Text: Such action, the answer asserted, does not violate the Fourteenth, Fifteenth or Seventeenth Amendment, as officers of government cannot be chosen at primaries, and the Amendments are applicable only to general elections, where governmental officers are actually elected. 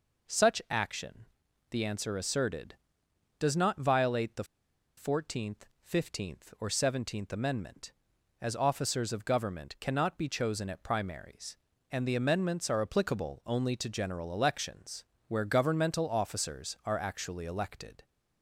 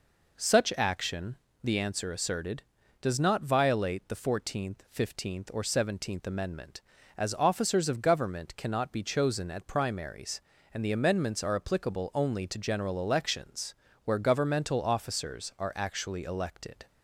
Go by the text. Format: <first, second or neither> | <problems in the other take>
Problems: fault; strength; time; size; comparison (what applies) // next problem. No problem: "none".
second | pauses between "the" and "Fourteenth"; noticeable; at 4.4 s; 0.53 s long